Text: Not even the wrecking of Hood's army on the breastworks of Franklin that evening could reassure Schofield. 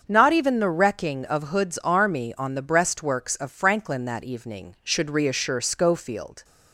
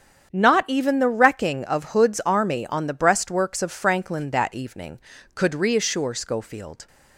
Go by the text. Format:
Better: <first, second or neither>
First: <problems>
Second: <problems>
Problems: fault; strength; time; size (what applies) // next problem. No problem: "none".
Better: second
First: starts louder than the rest; until 1.0 s; 7 dB // says "should" for "could"; at 4.8 s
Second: starts louder than the rest; strong; until 1.3 s; 8 dB